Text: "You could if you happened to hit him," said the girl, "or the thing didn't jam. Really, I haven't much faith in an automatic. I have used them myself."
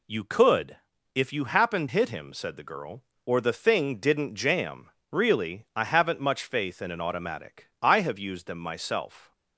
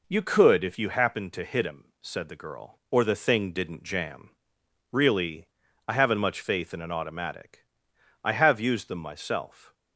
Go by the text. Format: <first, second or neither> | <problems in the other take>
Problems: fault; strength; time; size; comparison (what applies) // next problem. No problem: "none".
second | pauses between "could" and "if"; at 0.7 s; 0.40 s long // skips "to"; at 1.8 s